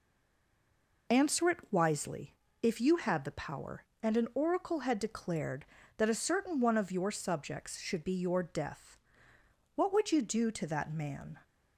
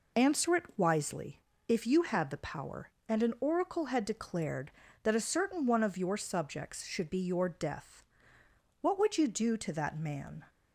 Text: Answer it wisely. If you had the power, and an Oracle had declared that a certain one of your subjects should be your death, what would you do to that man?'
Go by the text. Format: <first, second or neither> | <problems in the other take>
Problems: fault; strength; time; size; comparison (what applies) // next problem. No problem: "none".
second | stays silent before the first word; until 1.0 s; 1.0 s long